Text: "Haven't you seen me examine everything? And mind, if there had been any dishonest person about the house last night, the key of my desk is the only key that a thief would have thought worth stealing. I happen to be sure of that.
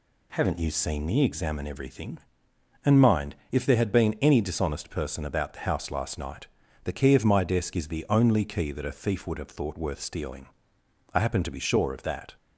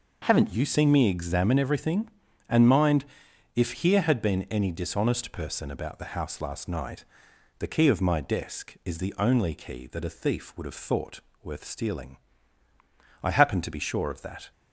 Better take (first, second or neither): first